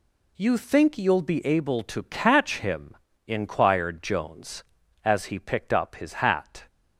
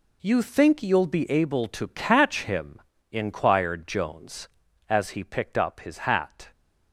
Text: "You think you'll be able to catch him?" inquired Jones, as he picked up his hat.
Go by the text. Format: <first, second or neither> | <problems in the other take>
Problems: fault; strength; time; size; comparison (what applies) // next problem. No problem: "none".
first | gets quieter; strong; throughout; 11 dB